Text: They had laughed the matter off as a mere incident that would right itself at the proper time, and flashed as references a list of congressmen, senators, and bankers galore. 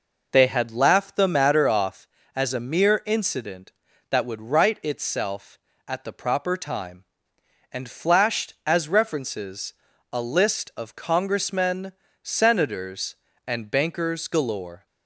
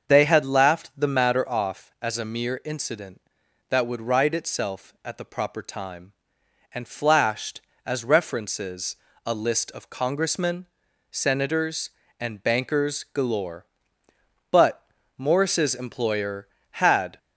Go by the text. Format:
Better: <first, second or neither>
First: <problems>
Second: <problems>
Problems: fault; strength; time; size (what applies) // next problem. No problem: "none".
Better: first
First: pauses between "references" and "a"; at 9.7 s; 0.38 s long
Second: starts louder than the rest; until 1.1 s; 6.5 dB // pauses between "references" and "a"; slight; at 8.9 s; 0.30 s long // goes on to say "But Morris's employer had"; strong; from 14.5 s on; 2.6 s long